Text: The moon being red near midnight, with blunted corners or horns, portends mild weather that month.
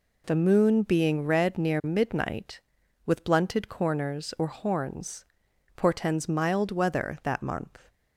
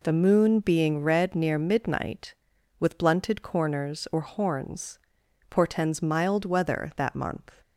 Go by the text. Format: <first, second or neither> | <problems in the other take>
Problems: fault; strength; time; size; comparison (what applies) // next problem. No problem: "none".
neither | none